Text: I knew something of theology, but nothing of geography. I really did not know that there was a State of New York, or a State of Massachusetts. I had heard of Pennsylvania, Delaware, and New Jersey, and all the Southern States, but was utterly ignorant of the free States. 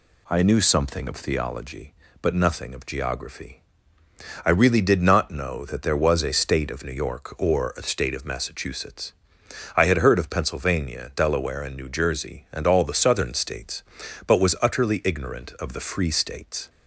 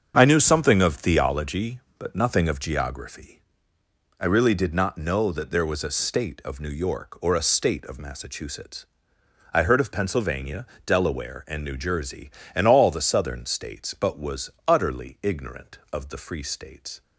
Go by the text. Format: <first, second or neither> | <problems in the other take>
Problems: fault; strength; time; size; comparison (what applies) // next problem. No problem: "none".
first | starts louder than the rest; until 1.1 s; 7 dB // skips "had"; at 9.6 s